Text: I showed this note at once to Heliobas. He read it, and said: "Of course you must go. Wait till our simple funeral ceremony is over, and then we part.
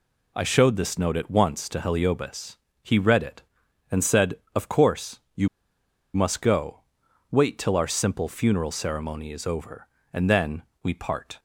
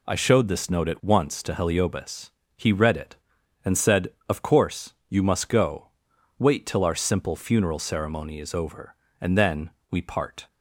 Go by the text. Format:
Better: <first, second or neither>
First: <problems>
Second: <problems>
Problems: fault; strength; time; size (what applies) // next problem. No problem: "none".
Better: second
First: pauses between "course" and "you"; slight; at 5.1 s; 0.16 s long // pauses between "you" and "must"; noticeable; at 5.4 s; 0.67 s long // pauses between "then" and "we"; slight; at 10.6 s; 0.20 s long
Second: pauses between "course" and "you"; slight; at 4.9 s; 0.16 s long // pauses between "then" and "we"; slight; at 9.7 s; 0.20 s long